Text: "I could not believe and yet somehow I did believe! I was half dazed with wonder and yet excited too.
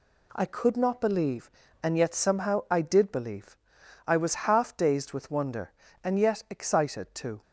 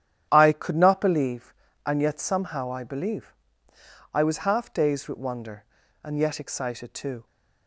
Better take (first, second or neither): first